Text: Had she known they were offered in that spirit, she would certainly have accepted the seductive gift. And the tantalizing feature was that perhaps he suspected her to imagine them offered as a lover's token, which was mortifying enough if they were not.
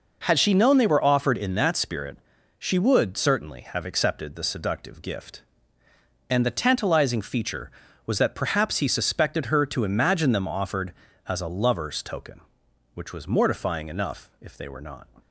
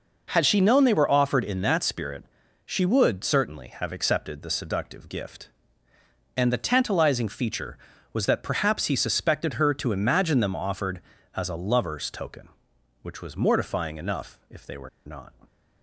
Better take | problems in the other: first | pauses between "were" and "not"; slight; at 14.8 s; 0.18 s long

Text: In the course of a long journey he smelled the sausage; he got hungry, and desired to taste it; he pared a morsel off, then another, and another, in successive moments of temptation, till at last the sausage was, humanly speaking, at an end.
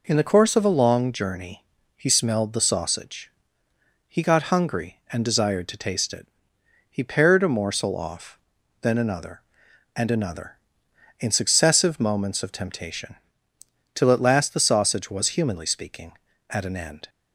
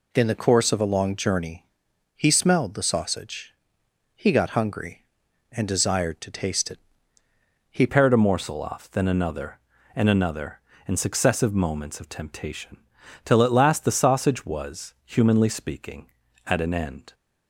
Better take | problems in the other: first | pauses between "journey" and "he"; noticeable; at 1.6 s; 0.52 s long; slight in the first // changes voice at "pared"; from 7.8 s on; 9.3 s long

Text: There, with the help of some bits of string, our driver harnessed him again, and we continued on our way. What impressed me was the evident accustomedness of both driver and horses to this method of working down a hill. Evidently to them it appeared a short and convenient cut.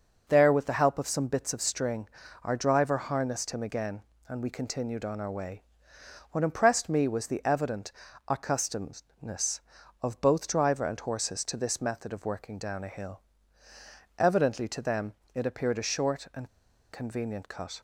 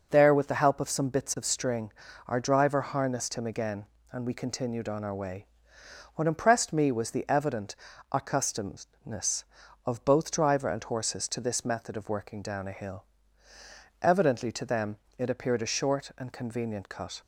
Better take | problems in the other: second | starts louder than the rest; noticeable; until 1.2 s; 6 dB; noticeable in the second // pauses between "evident" and "accustomedness"; slight; at 7.9 s; 0.36 s long; slight in the second // pauses between "them" and "it"; slight; at 15.1 s; 0.22 s long; slight in the second // pauses between "and" and "convenient"; at 16.4 s; 0.43 s long

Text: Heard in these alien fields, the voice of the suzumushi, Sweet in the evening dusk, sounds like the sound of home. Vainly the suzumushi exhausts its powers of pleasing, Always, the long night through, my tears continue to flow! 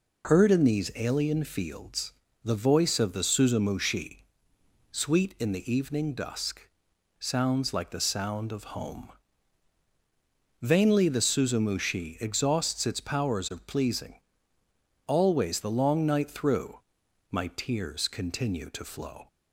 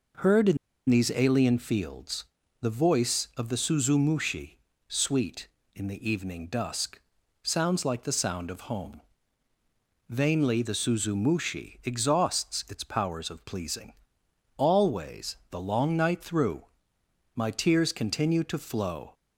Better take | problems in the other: first | pauses between "in" and "these"; slight; at 0.5 s; 0.32 s long

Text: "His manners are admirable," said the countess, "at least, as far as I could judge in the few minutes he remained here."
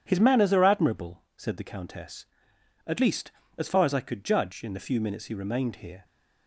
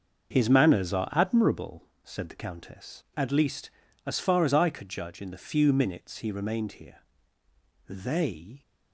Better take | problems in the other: first | starts louder than the rest; noticeable; until 1.3 s; 6 dB // goes on to say "They"; noticeable; from 7.8 s on; 0.72 s long

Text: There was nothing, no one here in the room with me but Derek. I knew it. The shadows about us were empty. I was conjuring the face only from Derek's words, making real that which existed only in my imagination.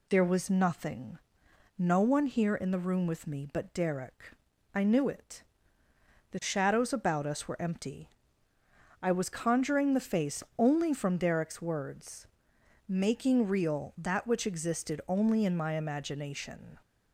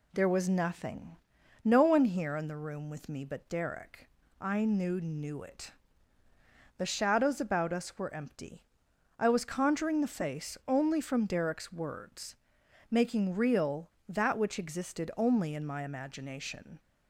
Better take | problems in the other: first | says "knew" twice; at 4.9 s

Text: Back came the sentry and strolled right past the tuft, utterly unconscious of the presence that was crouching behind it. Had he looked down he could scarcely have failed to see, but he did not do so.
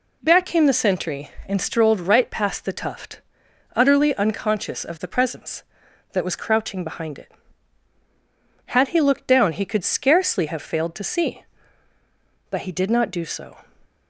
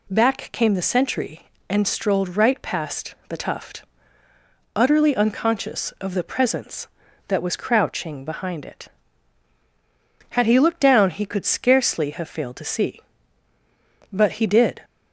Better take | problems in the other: first | stops before "not do so"; at 14.8 s

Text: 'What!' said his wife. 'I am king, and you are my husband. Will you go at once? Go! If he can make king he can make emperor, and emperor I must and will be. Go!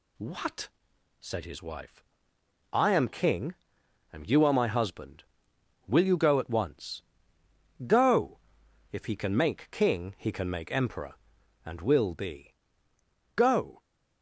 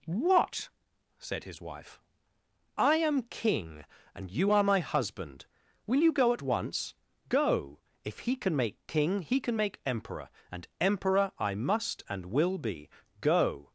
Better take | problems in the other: second | skips "and emperor I must"; at 11.3 s

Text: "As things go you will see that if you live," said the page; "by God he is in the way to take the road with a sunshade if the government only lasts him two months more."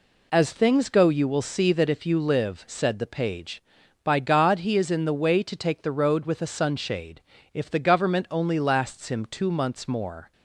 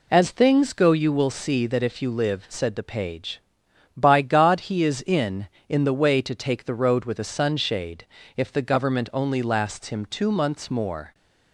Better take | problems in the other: first | says "in" twice; at 5.6 s // pauses between "sunshade" and "if"; slight; at 8.0 s; 0.28 s long; slight in the first

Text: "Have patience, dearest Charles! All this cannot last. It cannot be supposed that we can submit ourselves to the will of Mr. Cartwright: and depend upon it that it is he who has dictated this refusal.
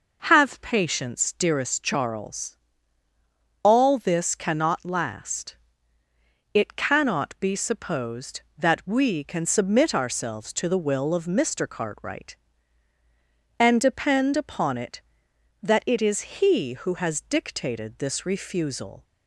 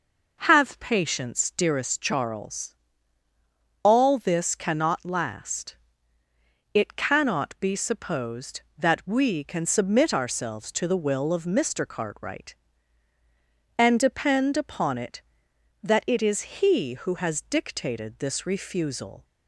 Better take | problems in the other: neither | none

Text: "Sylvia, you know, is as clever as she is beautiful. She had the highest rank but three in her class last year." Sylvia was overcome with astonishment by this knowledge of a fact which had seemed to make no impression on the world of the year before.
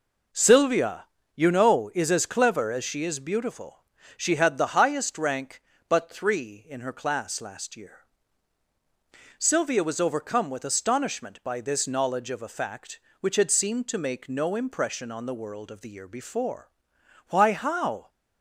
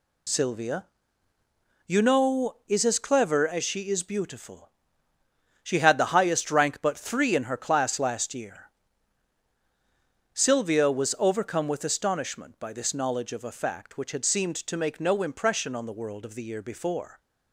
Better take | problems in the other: second | goes on to say "Why how"; noticeable; from 17.2 s on; 0.80 s long

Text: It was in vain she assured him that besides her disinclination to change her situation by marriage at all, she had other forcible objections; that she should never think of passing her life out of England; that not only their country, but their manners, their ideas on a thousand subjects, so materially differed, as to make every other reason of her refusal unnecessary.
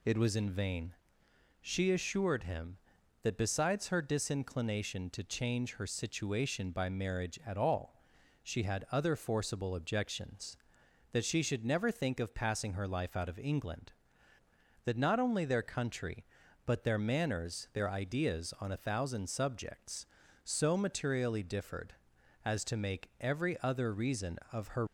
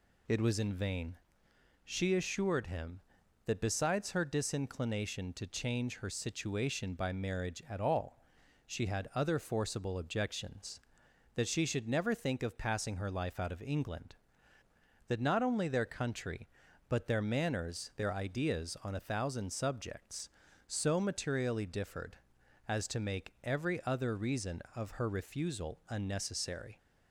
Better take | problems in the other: second | pauses between "vain" and "she"; noticeable; at 0.9 s; 0.66 s long; noticeable in the second // stops before "refusal unnecessary"; at 24.8 s

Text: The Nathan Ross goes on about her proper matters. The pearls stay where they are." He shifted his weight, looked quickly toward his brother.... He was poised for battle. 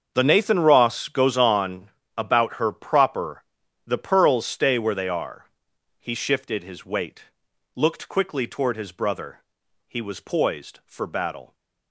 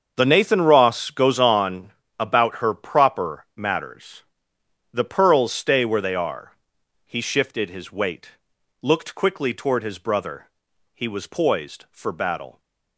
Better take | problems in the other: second | starts louder than the rest; until 1.1 s; 7 dB; also in the second // pauses between "on" and "about"; slight; at 1.9 s; 0.26 s long; slight in the second // skips "matters"; at 3.6 s

